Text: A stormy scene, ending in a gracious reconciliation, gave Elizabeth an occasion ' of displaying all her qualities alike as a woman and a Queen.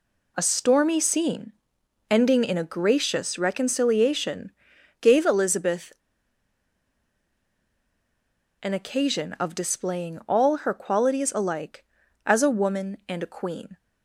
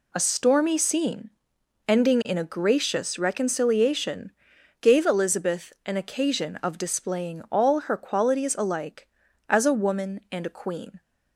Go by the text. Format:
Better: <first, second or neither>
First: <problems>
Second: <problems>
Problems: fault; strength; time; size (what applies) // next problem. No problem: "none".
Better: second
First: pauses between "Elizabeth" and "an"; strong; at 5.9 s; 2.6 s long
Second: none